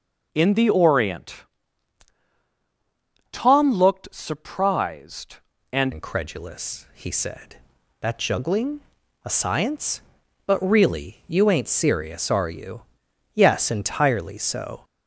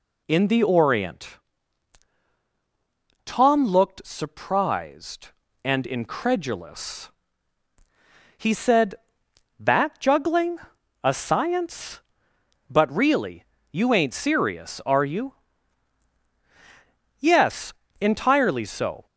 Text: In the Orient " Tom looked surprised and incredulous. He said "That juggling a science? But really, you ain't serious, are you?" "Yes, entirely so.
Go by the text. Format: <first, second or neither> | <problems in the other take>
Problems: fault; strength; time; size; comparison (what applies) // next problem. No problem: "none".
second | changes voice at "incredulous"; from 5.9 s on; 8.9 s long // pauses between "juggling" and "a"; at 8.8 s; 0.42 s long; also in the second